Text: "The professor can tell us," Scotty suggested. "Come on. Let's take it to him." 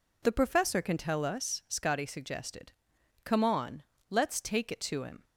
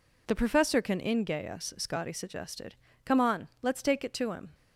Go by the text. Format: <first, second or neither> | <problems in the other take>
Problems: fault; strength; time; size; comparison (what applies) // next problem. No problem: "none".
first | says "ingay" for "tell"; at 0.9 s